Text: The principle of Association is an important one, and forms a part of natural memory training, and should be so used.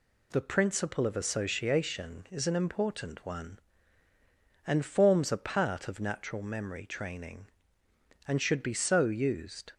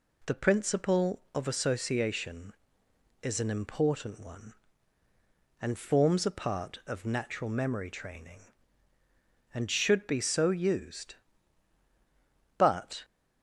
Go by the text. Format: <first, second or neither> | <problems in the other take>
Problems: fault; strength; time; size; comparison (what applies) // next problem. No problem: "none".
first | goes on to say "But"; slight; from 12.5 s on; 0.46 s long